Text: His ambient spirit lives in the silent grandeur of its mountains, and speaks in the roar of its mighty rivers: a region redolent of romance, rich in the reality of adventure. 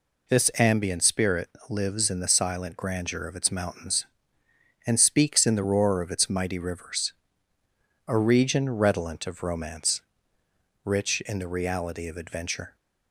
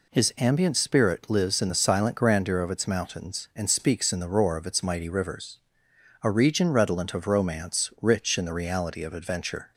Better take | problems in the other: second | says "This" for "His"; at 0.2 s // pauses between "spirit" and "lives"; slight; at 1.4 s; 0.20 s long

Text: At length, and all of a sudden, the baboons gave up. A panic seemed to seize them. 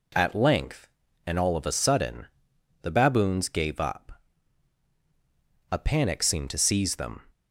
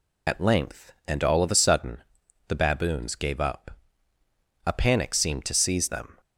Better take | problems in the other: first | loses the start of "At"; at 0.2 s; 75 ms

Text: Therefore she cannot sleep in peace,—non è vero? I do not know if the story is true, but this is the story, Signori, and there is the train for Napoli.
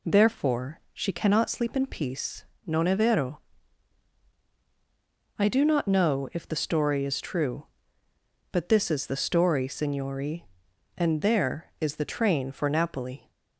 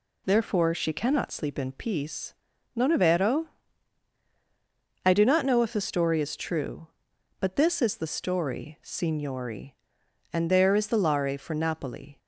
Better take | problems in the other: first | says "lare" for "train"; at 10.9 s

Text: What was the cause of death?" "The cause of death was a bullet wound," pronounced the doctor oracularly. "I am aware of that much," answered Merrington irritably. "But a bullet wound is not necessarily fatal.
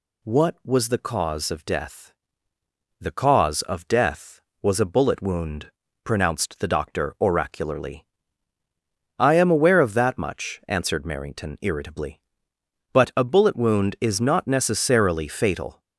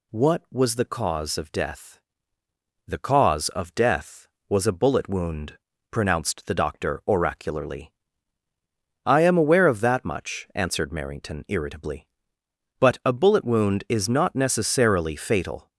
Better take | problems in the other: neither | none

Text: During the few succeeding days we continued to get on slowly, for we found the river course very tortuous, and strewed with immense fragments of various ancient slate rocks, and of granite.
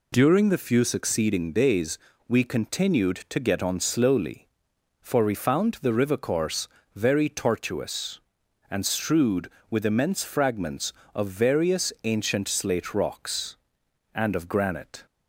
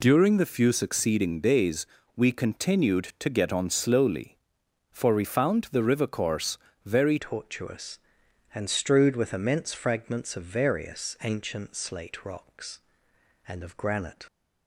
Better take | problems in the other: first | pauses between "days" and "we"; slight; at 1.8 s; 0.30 s long; slight in the first // pauses between "course" and "very"; slight; at 6.5 s; 0.26 s long; slight in the first // changes voice at "tortuous"; from 7.1 s on; 7.1 s long

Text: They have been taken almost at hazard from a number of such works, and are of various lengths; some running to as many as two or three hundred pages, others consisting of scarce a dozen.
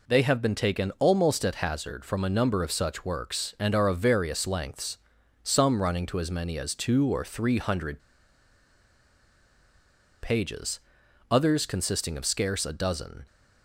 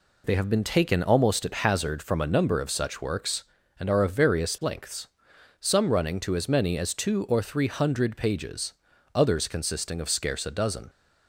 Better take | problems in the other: second | pauses between "hundred" and "pages"; strong; at 7.9 s; 2.2 s long

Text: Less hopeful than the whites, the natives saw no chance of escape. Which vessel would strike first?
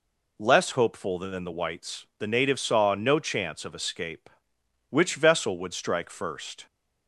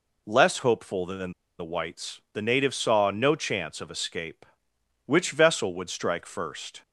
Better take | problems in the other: first | pauses between "than" and "the"; slight; at 1.3 s; 0.26 s long

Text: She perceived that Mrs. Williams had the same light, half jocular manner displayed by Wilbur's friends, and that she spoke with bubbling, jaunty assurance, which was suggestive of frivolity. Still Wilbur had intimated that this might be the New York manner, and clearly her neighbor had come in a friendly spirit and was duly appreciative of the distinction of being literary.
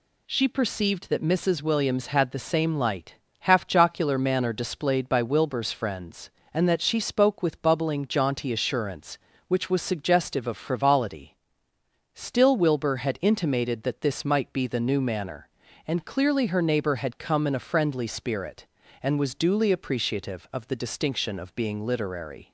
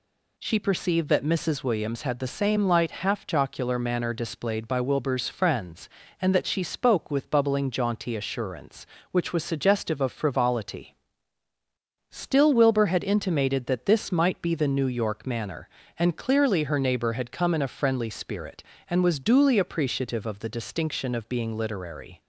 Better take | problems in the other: second | skips "York"; at 15.0 s

